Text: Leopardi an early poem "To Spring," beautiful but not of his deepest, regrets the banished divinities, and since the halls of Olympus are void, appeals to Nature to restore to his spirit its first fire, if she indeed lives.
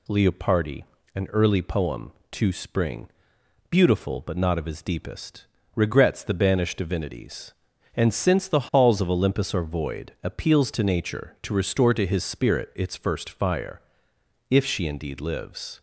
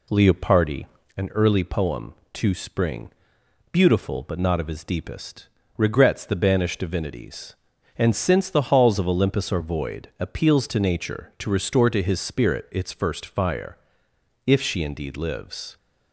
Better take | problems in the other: first | starts louder than the rest; slight; until 1.2 s; 2.5 dB // pauses between "Leopardi" and "an"; slight; at 0.8 s; 0.32 s long; slight in the first

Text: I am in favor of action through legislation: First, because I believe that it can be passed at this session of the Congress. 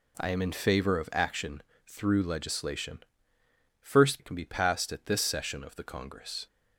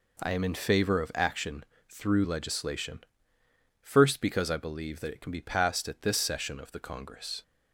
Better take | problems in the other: second | pauses between "action" and "through"; slight; at 1.6 s; 0.24 s long; slight in the second // skips "because I believe that"; at 4.1 s

